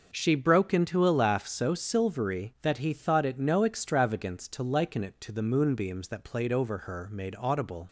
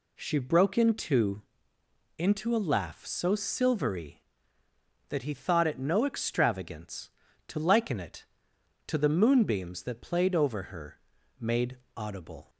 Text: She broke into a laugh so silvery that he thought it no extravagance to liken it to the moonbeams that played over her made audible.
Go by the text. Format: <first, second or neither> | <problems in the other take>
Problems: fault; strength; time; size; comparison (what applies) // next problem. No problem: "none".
first | says "into" twice; at 2.1 s // pauses between "her" and "made"; at 10.9 s; 0.40 s long // pauses between "made" and "audible"; slight; at 11.7 s; 0.18 s long